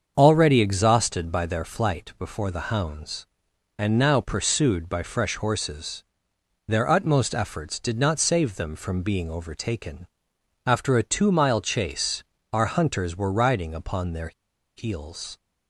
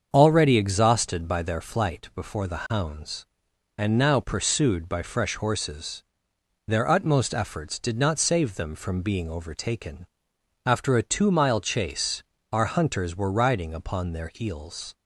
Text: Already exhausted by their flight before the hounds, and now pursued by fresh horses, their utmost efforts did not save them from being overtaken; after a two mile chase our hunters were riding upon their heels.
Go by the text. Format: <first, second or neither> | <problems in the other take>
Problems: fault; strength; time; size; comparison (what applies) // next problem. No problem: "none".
second | starts louder than the rest; until 1.1 s; 7 dB; also in the second // pauses between "chase" and "our"; slight; at 12.2 s; 0.30 s long; slight in the second // pauses between "their" and "heels"; at 14.3 s; 0.45 s long